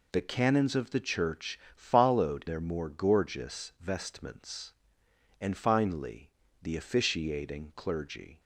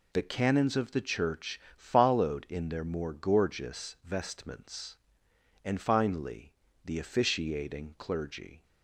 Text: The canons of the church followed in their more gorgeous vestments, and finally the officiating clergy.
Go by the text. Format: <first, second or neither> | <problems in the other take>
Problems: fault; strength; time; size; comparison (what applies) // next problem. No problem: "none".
second | pauses between "church" and "followed"; slight; at 1.5 s; 0.16 s long; slight in the second // skips "in"; at 2.4 s // pauses between "finally" and "the"; slight; at 6.2 s; 0.32 s long; slight in the second